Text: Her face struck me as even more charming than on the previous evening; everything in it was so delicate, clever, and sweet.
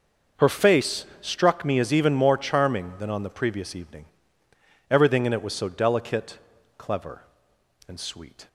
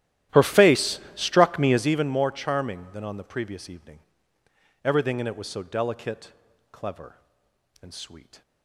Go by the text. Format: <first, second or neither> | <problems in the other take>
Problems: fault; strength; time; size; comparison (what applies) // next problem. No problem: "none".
first | starts louder than the rest; strong; until 2.0 s; 13 dB // pauses between "face" and "struck"; slight; at 0.9 s; 0.16 s long; slight in the first